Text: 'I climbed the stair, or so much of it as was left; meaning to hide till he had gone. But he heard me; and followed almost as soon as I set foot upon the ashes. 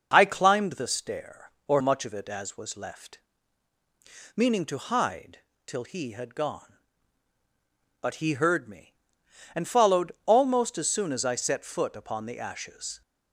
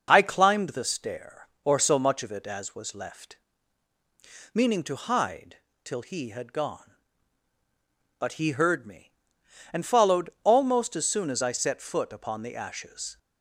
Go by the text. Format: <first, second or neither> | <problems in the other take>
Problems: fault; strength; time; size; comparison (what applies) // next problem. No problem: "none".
second | skips "so"; at 1.8 s // pauses between "hide" and "till"; slight; at 5.3 s; 0.26 s long; slight in the second